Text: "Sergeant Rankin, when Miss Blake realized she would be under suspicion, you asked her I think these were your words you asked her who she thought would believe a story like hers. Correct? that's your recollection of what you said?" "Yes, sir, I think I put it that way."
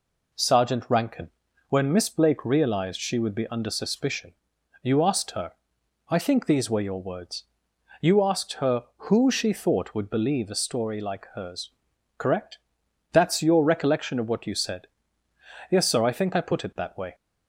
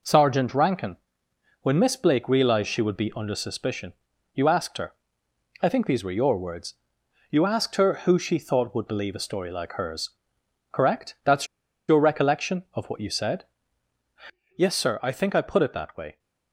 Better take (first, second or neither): first